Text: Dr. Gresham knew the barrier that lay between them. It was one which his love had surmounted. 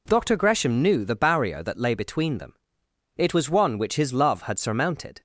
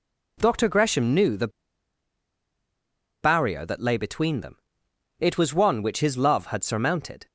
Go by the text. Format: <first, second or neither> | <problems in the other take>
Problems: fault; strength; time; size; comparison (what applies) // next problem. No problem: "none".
first | pauses between "the" and "barrier"; strong; at 1.4 s; 1.7 s long